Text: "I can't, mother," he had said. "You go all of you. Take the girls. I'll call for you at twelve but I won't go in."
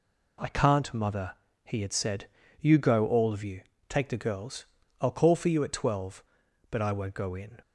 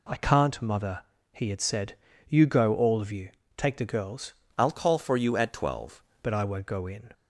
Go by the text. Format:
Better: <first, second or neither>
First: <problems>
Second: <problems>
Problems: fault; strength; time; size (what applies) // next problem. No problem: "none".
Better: first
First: none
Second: changes voice from "I'll" to "twelve"; from 4.5 to 6.0 s; 1.5 s long